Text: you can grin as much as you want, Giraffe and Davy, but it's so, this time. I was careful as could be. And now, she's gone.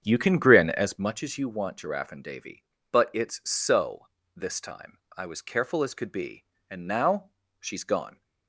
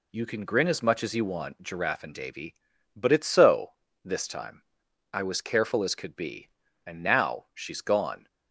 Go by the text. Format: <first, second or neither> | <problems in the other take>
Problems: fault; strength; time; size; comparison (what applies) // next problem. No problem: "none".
second | starts louder than the rest; strong; until 1.3 s; 8 dB